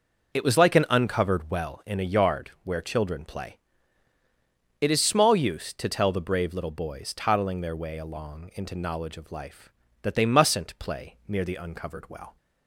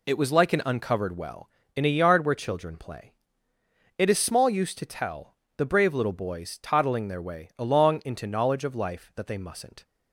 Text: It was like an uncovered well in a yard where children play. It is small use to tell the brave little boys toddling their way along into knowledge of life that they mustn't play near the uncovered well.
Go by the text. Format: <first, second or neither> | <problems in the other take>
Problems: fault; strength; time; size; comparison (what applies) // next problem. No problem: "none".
first | pauses between "tell" and "the"; slight; at 5.3 s; 0.22 s long // stops before "play near the uncovered well"; at 9.8 s